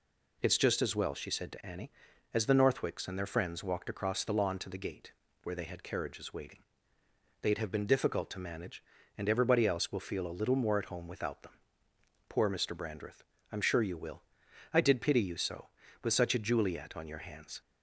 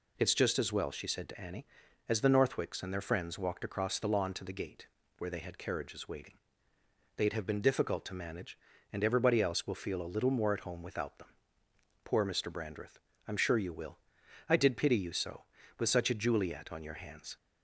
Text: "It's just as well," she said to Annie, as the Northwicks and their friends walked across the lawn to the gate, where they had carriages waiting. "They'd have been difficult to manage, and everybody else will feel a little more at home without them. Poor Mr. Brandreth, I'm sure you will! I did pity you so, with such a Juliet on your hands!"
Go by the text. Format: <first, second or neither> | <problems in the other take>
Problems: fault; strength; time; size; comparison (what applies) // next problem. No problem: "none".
neither | none